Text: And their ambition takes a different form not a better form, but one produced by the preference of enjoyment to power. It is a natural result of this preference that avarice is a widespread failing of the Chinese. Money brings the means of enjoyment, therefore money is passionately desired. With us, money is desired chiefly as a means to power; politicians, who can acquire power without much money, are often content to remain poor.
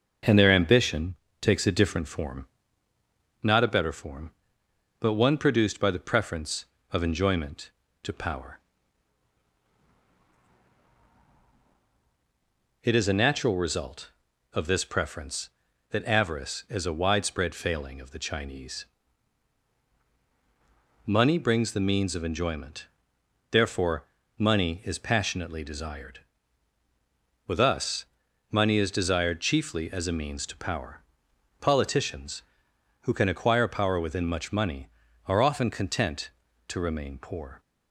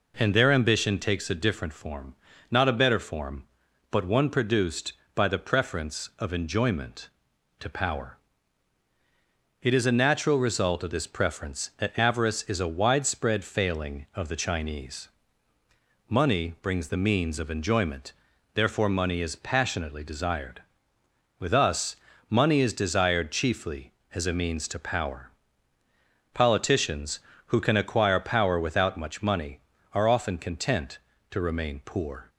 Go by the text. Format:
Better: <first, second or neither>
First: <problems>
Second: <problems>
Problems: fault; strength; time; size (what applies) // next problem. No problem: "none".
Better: second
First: pauses between "ambition" and "takes"; slight; at 1.1 s; 0.24 s long // pauses between "form" and "not"; at 2.4 s; 1.0 s long // pauses between "therefore" and "money"; slight; at 24.0 s; 0.32 s long // says "within" for "without"; at 33.9 s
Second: pauses between "form" and "not"; slight; at 2.1 s; 0.36 s long